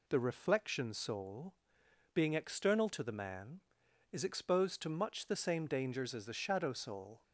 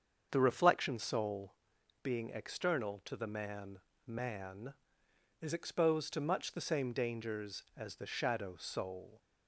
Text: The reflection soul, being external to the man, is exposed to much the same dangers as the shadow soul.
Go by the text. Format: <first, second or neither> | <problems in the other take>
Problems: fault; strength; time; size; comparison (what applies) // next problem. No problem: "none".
first | starts louder than the rest; until 1.3 s; 7 dB // says "man" twice; at 4.0 s